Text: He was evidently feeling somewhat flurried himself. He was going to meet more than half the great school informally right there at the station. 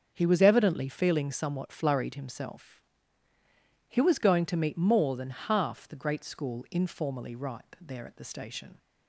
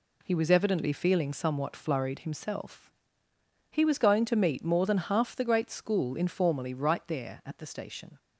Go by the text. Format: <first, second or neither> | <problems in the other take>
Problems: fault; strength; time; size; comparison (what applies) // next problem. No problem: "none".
second | starts louder than the rest; until 1.1 s; 6.5 dB // says "ripe" for "right"; at 7.3 s